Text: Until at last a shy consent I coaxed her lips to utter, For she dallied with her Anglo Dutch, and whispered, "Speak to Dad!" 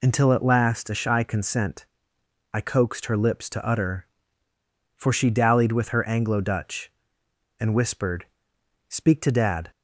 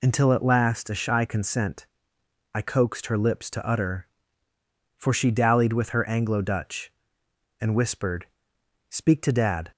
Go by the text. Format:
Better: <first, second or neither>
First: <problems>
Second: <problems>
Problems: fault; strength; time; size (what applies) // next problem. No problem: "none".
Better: neither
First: pauses between "consent" and "I"; noticeable; at 1.8 s; 0.68 s long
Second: pauses between "consent" and "I"; noticeable; at 1.8 s; 0.68 s long